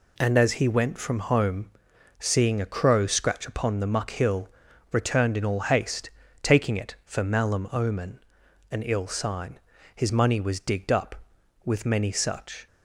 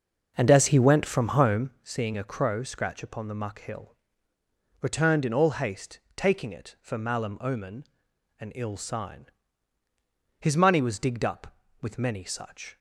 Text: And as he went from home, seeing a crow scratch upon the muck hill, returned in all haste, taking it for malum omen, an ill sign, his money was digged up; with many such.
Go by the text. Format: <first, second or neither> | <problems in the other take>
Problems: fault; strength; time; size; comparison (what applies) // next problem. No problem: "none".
first | starts louder than the rest; noticeable; until 1.8 s; 6 dB